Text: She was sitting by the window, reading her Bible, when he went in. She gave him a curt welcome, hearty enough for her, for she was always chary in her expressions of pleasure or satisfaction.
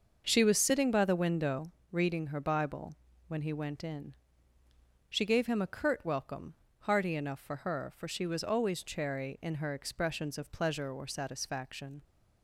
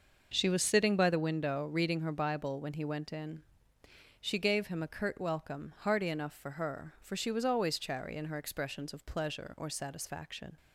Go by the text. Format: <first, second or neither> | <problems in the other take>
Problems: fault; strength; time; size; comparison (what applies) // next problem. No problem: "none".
neither | starts louder than the rest; the same in both